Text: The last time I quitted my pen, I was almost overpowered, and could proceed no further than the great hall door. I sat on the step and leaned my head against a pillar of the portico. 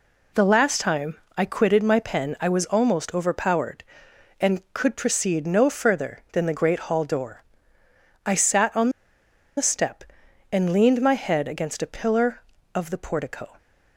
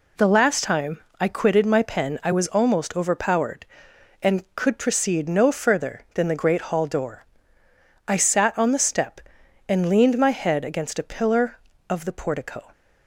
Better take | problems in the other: second | pauses between "time" and "I"; slight; at 1.1 s; 0.18 s long; slight in the second // pauses between "on" and "the"; noticeable; at 8.8 s; 0.68 s long

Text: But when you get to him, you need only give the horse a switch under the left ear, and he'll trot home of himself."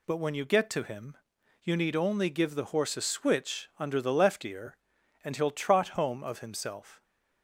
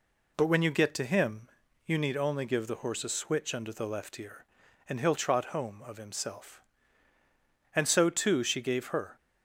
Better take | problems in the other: first | goes on to say "And so too she gave her"; from 7.7 s on; 1.4 s long

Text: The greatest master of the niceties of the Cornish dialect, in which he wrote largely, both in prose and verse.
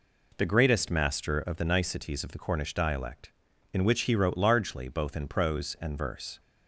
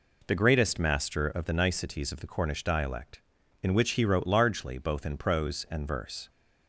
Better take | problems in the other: neither | none

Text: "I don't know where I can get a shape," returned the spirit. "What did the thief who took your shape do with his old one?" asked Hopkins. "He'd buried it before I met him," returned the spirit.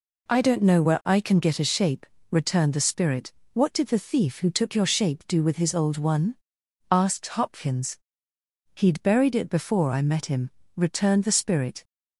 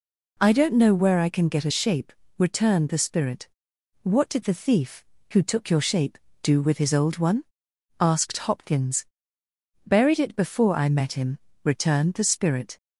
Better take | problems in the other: first | skips "He'd"; at 9.4 s

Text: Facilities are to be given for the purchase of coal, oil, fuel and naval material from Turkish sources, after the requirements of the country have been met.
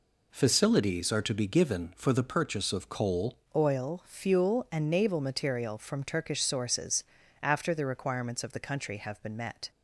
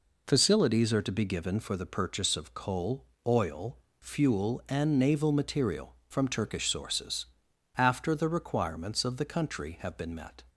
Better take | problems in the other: second | changes voice at "oil"; from 3.5 s on; 6.2 s long

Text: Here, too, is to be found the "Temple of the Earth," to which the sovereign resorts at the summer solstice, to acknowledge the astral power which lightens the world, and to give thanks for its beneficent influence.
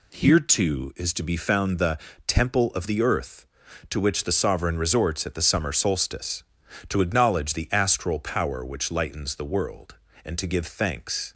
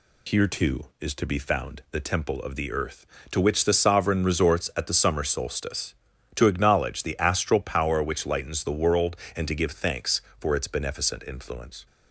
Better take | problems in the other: second | pauses between "the" and "Temple"; slight; at 1.9 s; 0.30 s long // stops before "for its beneficent influence"; at 11.3 s

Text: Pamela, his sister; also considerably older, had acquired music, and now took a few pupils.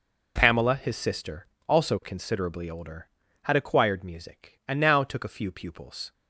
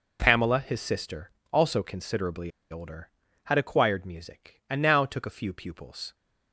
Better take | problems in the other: first | pauses between "considerably" and "older"; slight; at 2.5 s; 0.20 s long

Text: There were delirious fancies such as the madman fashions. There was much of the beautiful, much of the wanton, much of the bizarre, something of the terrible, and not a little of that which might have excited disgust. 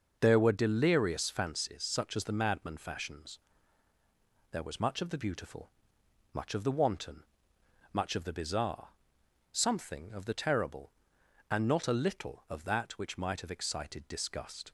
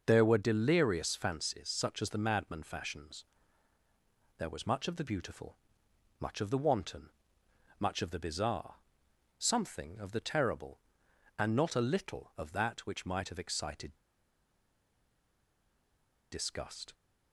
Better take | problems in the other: first | pauses between "excited" and "disgust"; strong; at 13.9 s; 2.3 s long

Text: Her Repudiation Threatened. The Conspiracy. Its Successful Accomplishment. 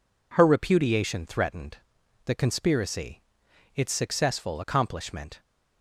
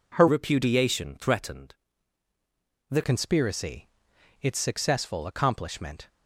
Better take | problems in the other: first | changes voice from "Repudiation" to "The"; from 0.2 to 3.0 s; 2.8 s long

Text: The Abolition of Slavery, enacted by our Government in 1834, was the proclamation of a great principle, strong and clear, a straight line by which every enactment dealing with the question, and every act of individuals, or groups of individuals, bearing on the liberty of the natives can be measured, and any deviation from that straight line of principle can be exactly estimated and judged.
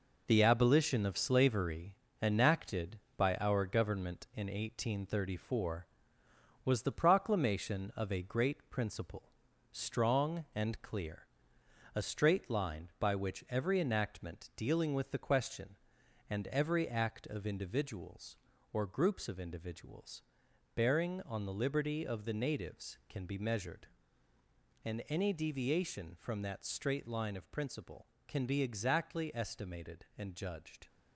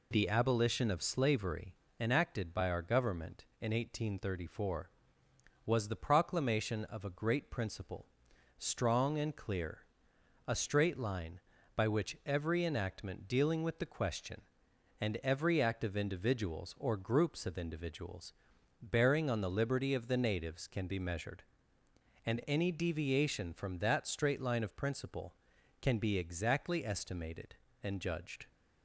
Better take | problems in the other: second | gets quieter; throughout; 6.5 dB

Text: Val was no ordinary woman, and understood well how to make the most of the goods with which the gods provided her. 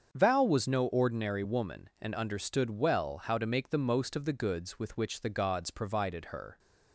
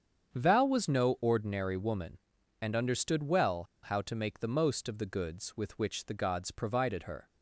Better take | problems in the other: first | starts louder than the rest; strong; until 1.3 s; 7.5 dB; strong in the first // pauses between "well" and "how"; slight; at 3.6 s; 0.20 s long

